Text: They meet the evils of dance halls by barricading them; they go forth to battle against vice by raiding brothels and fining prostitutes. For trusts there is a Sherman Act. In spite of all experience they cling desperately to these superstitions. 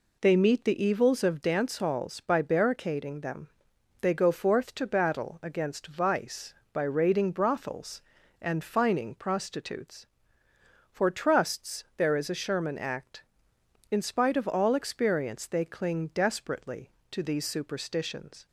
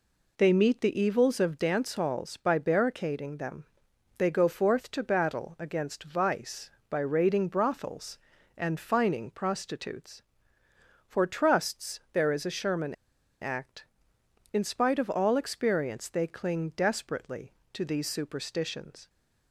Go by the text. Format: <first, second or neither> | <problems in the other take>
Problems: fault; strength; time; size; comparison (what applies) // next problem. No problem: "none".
first | pauses between "Sherman" and "Act"; noticeable; at 12.9 s; 0.46 s long